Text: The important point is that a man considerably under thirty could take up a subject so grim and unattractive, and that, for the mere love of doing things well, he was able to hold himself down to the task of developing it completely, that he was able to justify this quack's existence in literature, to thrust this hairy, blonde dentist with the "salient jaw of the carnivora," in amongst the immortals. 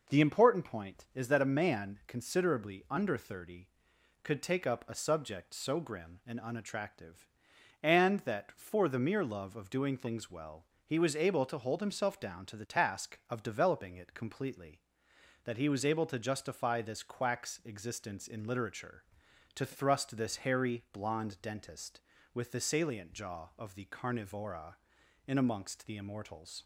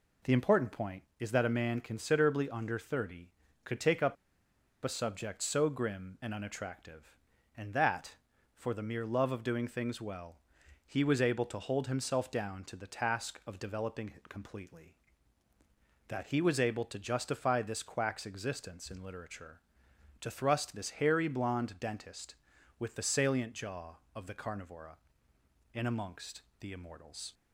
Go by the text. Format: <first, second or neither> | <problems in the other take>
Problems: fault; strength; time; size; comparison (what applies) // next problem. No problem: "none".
first | pauses between "up" and "a"; noticeable; at 4.1 s; 0.68 s long // pauses between "amongst" and "the"; slight; at 26.4 s; 0.18 s long